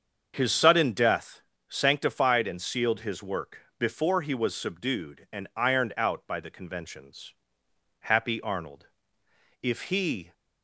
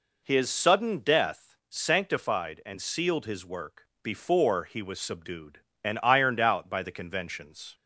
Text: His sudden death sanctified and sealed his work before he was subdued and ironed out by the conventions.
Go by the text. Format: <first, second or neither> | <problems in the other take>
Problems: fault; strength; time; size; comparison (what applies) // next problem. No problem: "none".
second | starts louder than the rest; until 1.3 s; 7 dB // pauses between "death" and "sanctified"; slight; at 1.4 s; 0.26 s long // pauses between "work" and "before"; slight; at 3.5 s; 0.20 s long; slight in the second // goes on to say "Happy Arnold If he"; strong; from 8.0 s on; 2.3 s long